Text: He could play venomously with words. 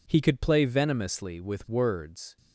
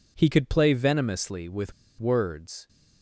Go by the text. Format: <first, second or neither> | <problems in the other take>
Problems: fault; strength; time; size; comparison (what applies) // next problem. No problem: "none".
first | pauses between "with" and "words"; slight; at 1.7 s; 0.27 s long